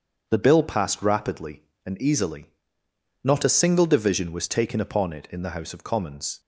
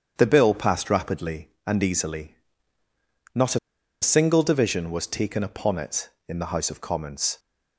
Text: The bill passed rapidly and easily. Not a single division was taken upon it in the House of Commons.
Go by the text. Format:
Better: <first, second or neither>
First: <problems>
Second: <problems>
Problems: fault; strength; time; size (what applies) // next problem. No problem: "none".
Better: first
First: starts louder than the rest; strong; until 1.2 s; 7.5 dB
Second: starts louder than the rest; strong; until 1.1 s; 8.5 dB // pauses between "a" and "single"; at 3.5 s; 0.43 s long